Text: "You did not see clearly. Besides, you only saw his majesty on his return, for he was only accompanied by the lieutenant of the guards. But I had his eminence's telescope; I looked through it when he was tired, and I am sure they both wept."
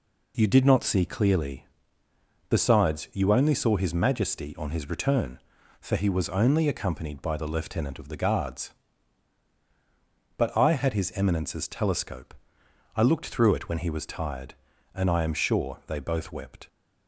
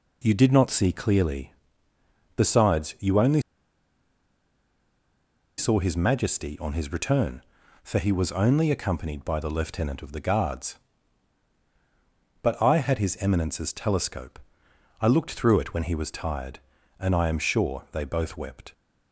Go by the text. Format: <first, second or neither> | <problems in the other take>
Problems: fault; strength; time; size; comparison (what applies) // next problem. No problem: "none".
first | pauses between "only" and "saw"; strong; at 3.4 s; 2.1 s long